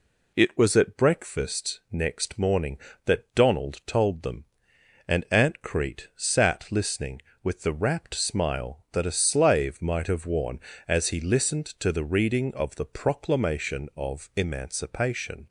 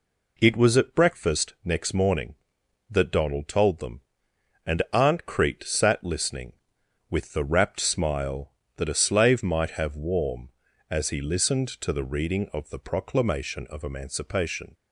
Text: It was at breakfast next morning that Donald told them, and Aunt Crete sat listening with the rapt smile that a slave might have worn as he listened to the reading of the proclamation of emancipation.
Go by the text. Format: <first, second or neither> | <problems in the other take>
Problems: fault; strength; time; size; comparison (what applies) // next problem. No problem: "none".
first | says "warm" for "worn"; at 9.9 s